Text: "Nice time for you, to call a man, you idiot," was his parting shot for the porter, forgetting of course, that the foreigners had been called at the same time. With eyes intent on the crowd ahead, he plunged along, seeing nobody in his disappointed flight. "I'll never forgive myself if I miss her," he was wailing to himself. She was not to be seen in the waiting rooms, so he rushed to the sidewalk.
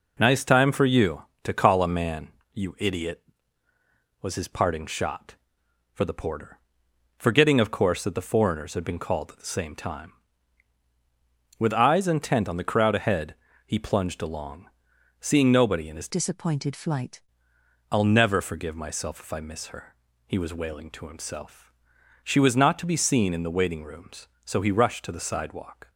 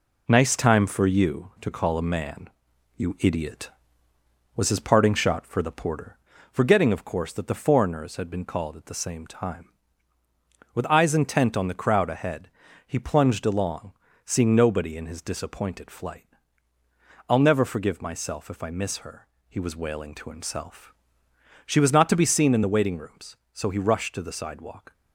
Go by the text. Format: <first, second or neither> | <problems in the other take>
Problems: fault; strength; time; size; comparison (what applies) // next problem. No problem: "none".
second | changes voice from "disappointed" to "flight"; from 16.0 to 17.2 s; 1.2 s long